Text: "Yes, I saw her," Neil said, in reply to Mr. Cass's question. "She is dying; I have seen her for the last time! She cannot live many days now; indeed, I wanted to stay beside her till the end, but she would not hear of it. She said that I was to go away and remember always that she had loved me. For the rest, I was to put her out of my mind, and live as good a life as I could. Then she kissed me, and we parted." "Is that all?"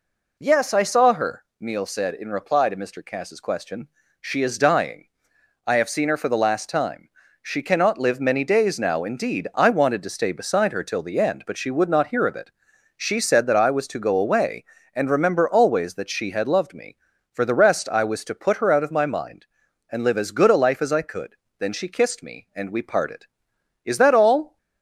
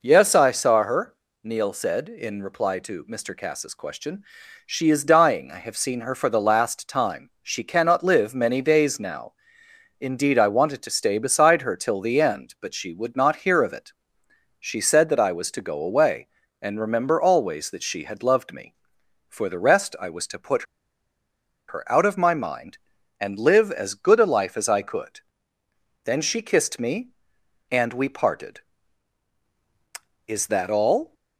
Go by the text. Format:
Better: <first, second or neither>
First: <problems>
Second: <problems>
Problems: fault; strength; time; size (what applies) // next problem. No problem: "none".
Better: first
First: none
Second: pauses between "put" and "her"; at 20.6 s; 1.0 s long